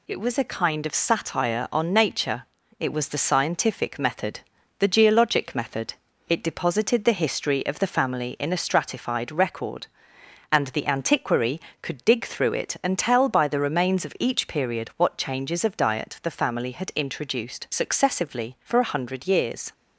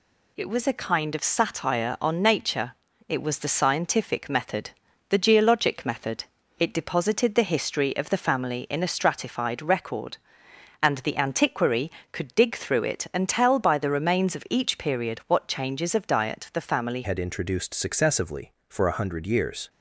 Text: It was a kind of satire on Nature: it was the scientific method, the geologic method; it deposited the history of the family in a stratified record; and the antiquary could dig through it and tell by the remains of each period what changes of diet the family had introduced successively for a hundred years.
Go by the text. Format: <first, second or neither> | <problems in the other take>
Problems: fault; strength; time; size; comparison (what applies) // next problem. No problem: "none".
first | changes voice at "had"; from 17.0 s on; 2.6 s long